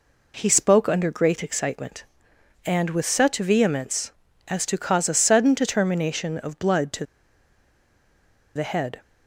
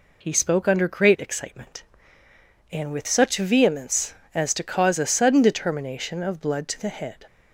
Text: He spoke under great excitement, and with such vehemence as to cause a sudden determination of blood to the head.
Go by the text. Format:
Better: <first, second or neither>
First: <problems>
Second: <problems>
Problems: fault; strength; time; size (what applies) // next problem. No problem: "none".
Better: second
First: pauses between "to" and "the"; strong; at 7.0 s; 1.5 s long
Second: none